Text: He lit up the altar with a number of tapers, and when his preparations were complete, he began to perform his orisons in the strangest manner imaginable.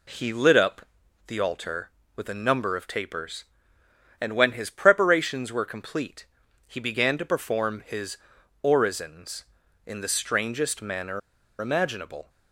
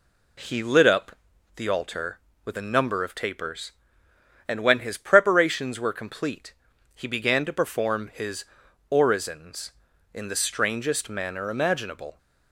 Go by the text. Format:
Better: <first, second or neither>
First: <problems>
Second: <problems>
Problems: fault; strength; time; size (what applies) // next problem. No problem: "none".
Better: second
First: pauses between "up" and "the"; at 0.8 s; 0.40 s long // pauses between "his" and "orisons"; noticeable; at 8.1 s; 0.48 s long // pauses between "manner" and "imaginable"; at 11.2 s; 0.40 s long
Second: pauses between "up" and "the"; at 1.1 s; 0.38 s long // pauses between "his" and "orisons"; noticeable; at 8.4 s; 0.48 s long